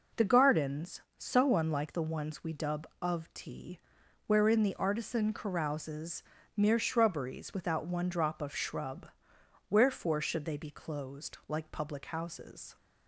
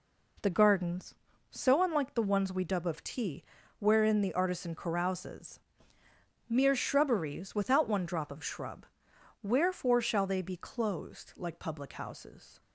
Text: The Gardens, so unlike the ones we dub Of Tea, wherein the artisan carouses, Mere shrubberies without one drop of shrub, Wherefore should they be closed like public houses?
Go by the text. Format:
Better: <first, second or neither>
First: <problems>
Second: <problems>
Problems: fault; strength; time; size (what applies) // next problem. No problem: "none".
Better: first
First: none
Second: says "shall" for "should"; at 10.0 s